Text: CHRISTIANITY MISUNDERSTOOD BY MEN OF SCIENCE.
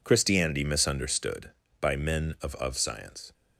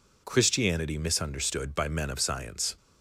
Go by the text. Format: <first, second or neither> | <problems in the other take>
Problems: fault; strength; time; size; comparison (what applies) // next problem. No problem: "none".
second | says "OF" twice; at 2.5 s